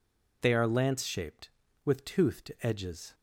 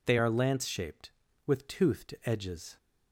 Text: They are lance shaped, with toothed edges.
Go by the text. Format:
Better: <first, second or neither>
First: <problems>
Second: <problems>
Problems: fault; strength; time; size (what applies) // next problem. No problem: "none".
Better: neither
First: none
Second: none